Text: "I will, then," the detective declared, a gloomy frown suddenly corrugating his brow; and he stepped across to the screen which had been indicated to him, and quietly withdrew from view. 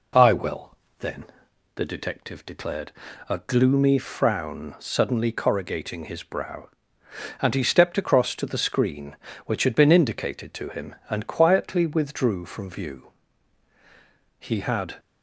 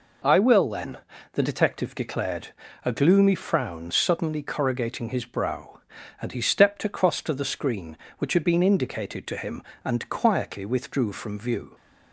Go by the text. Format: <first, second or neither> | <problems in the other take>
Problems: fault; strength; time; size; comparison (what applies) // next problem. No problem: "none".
second | goes on to say "He had"; from 14.3 s on; 0.60 s long